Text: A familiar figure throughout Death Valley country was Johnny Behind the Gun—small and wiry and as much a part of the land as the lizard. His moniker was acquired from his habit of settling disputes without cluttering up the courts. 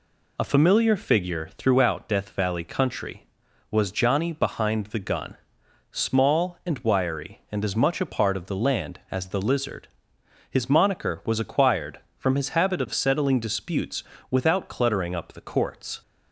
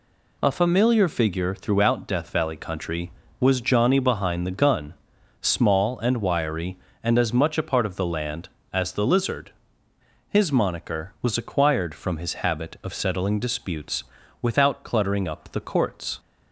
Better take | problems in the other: neither | pauses between "disputes" and "without"; slight; the same in both

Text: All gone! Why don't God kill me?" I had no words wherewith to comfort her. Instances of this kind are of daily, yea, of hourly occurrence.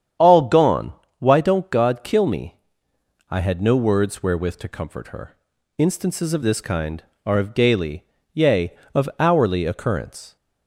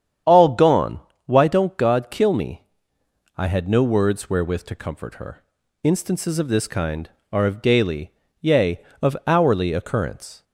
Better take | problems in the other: neither | starts louder than the rest; strong; the same in both

